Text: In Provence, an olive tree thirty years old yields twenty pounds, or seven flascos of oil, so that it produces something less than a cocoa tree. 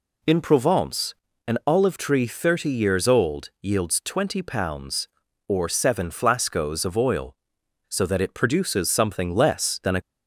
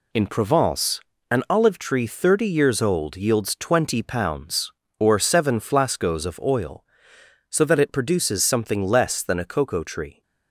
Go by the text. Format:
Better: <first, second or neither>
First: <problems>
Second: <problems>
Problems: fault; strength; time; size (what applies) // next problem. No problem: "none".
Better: second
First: stops before "cocoa tree"; at 10.0 s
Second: none